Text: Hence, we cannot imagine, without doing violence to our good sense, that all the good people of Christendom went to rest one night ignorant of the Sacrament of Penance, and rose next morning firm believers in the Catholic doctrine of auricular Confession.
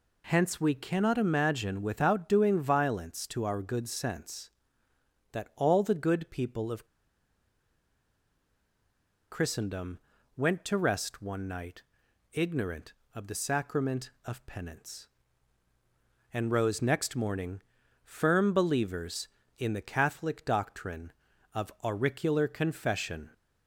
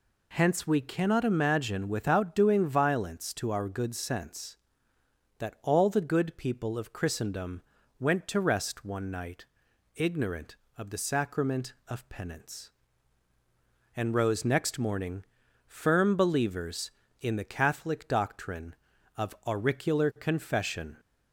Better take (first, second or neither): second